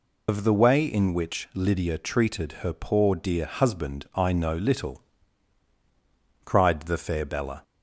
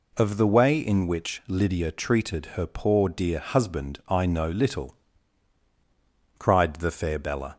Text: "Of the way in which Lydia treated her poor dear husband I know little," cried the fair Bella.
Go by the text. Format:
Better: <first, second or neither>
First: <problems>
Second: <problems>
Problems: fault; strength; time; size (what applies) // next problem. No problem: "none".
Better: second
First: loses the start of "Of"; at 0.2 s; 90 ms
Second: none